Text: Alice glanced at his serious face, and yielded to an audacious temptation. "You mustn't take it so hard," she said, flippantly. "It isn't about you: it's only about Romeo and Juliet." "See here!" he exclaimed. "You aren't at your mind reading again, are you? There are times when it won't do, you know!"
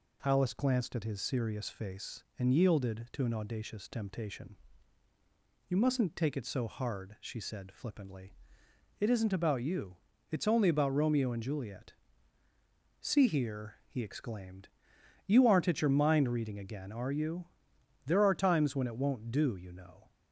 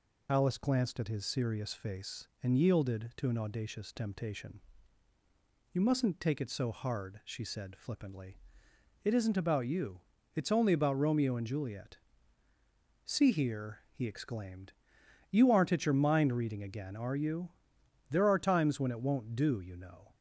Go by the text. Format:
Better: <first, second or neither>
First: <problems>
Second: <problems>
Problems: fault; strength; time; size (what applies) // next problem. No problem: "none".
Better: first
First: none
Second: loses the start of "Alice"; at 0.2 s; 45 ms